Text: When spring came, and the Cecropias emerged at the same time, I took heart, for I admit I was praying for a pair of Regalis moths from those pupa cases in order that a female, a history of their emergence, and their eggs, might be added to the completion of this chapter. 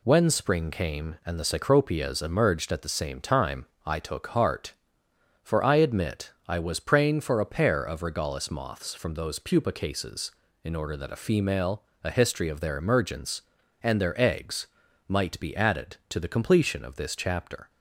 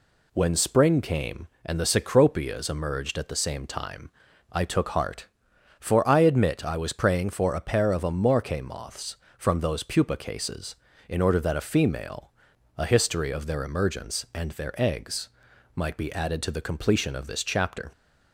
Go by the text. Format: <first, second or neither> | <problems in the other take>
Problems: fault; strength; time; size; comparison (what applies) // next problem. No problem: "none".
first | says "Amorque" for "Regalis"; at 8.0 s